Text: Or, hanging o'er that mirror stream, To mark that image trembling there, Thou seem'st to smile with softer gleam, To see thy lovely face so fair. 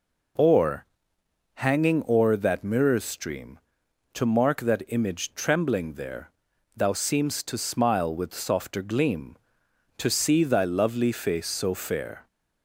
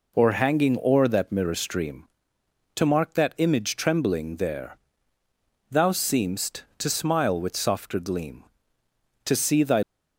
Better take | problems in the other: first | stops before "lovely face so fair"; at 9.8 s

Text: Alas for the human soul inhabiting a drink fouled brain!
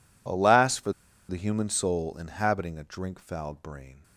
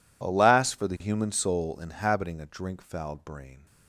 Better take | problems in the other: second | pauses between "for" and "the"; at 0.9 s; 0.38 s long

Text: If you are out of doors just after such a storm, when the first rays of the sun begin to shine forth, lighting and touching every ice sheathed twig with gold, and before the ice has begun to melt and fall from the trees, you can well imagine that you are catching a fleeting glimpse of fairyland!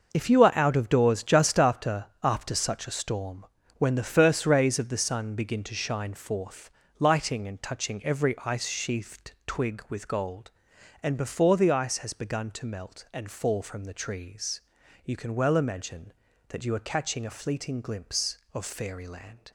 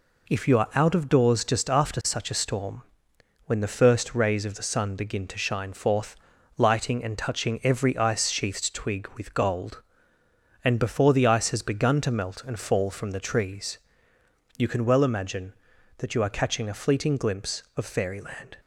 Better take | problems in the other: second | says "after" twice; at 2.2 s // pauses between "sheathed" and "twig"; slight; at 9.3 s; 0.16 s long

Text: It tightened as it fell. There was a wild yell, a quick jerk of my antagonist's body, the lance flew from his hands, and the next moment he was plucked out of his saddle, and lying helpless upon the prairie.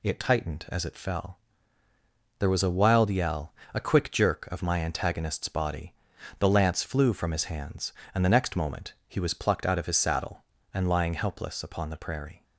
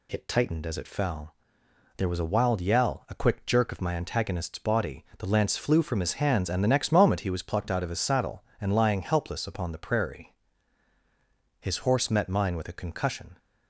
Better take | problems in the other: first | goes on to say "His horse met mine with a concussion"; strong; from 11.6 s on; 1.7 s long

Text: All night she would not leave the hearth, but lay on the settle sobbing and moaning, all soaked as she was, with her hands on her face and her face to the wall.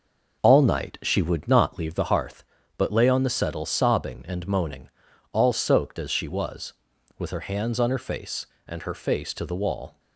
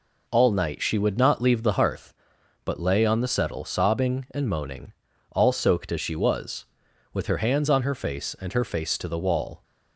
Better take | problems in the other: second | starts louder than the rest; noticeable; until 1.9 s; 5.5 dB

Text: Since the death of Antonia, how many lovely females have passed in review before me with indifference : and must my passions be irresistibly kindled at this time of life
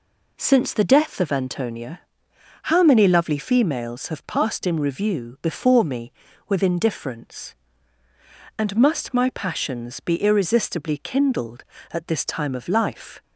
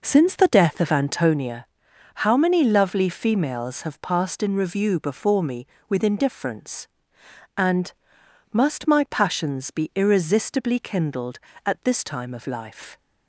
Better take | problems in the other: first | starts louder than the rest; noticeable; until 1.4 s; 5.5 dB // pauses between "and" and "must"; noticeable; at 7.9 s; 0.58 s long

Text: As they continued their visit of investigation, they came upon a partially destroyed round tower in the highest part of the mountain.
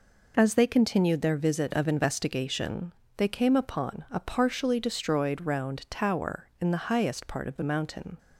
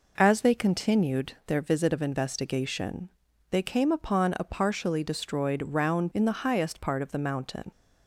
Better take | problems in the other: first | skips "tower"; at 6.1 s

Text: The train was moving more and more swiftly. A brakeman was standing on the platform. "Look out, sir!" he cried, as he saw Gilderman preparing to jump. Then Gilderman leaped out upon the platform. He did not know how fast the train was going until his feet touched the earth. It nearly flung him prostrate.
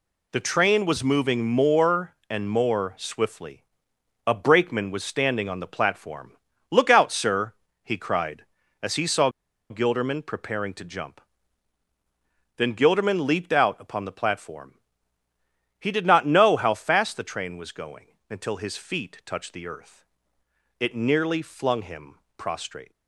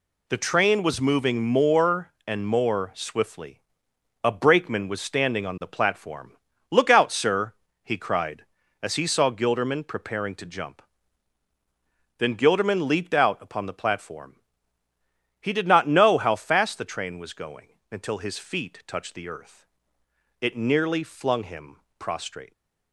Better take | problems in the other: second | pauses between "saw" and "Gilderman"; at 9.2 s; 0.40 s long // pauses between "him" and "prostrate"; slight; at 22.1 s; 0.20 s long; slight in the second

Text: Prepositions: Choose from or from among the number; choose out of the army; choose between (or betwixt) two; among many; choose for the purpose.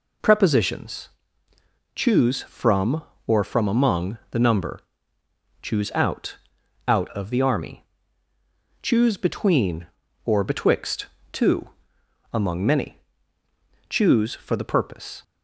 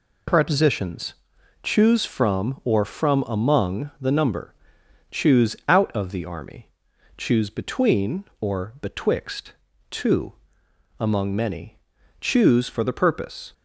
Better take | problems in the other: second | says "out" twice; at 6.8 s

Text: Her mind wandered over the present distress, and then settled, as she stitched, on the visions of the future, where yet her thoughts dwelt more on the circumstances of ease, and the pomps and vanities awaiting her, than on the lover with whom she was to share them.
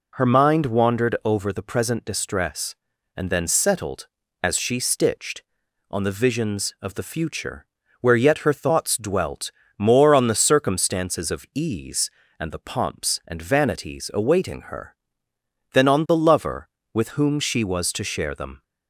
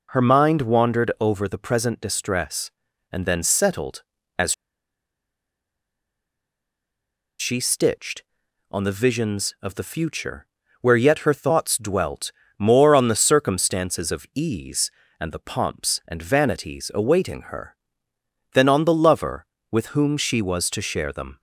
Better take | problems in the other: first | pauses between "as" and "she"; strong; at 4.5 s; 2.8 s long // pauses between "dwelt" and "more"; slight; at 12.3 s; 0.26 s long; slight in the first

